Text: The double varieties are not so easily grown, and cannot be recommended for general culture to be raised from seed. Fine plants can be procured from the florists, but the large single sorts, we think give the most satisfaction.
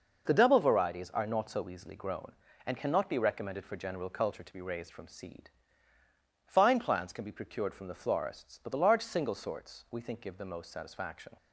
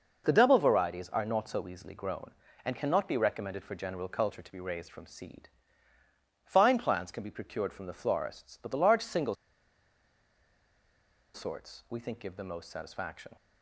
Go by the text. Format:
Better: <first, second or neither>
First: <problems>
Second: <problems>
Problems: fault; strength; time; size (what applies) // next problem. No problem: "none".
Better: first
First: none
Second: pauses between "single" and "sorts"; strong; at 9.3 s; 1.9 s long